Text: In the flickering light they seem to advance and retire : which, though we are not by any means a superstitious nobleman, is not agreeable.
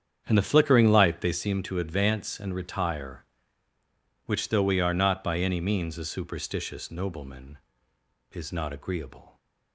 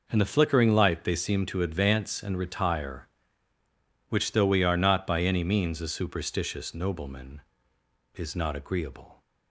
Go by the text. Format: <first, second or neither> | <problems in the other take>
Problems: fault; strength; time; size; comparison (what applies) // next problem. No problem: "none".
second | starts louder than the rest; strong; until 1.4 s; 8 dB